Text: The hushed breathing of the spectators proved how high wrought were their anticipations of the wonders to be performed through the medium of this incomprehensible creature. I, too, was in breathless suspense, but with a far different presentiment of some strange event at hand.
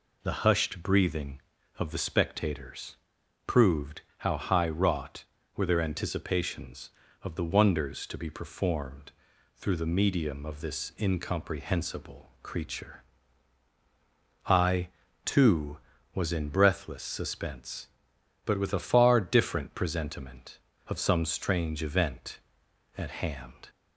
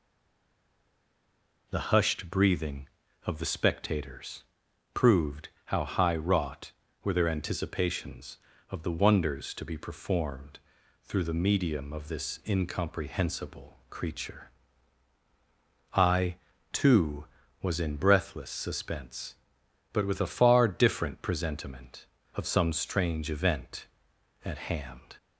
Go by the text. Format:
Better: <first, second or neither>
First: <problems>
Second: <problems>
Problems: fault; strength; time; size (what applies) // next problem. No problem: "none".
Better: first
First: pauses between "spectators" and "proved"; noticeable; at 2.9 s; 0.50 s long // pauses between "proved" and "how"; slight; at 4.0 s; 0.18 s long // pauses between "performed" and "through"; at 9.1 s; 0.42 s long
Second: stays silent before the first word; noticeable; until 1.6 s; 1.6 s long // pauses between "spectators" and "proved"; noticeable; at 4.4 s; 0.50 s long // pauses between "proved" and "how"; slight; at 5.4 s; 0.18 s long // pauses between "performed" and "through"; at 10.5 s; 0.42 s long